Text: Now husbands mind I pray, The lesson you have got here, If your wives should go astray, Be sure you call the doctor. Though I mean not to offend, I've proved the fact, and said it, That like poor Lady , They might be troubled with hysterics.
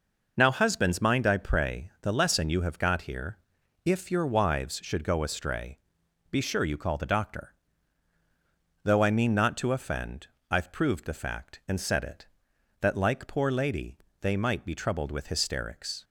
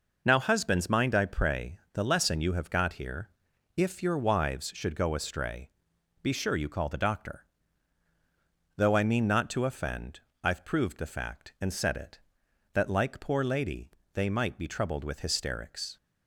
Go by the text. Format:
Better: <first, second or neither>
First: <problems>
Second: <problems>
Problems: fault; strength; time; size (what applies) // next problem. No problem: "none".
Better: neither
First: none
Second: none